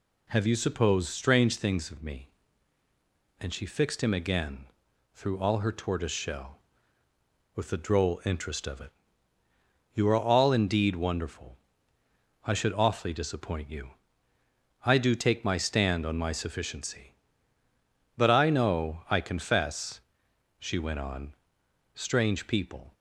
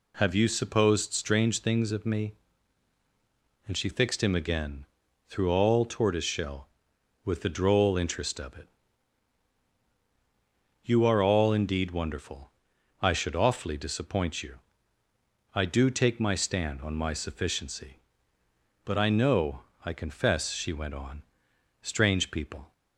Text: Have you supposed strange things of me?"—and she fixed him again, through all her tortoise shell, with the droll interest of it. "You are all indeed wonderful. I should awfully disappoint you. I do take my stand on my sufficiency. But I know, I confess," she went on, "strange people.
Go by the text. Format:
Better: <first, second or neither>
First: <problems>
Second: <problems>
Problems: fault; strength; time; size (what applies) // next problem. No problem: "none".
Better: first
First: none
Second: skips "her"; at 5.8 s